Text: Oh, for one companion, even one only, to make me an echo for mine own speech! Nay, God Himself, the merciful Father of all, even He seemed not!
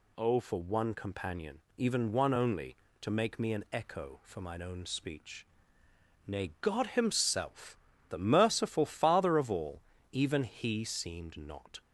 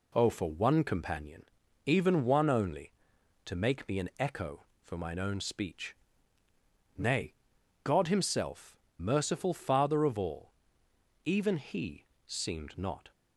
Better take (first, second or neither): first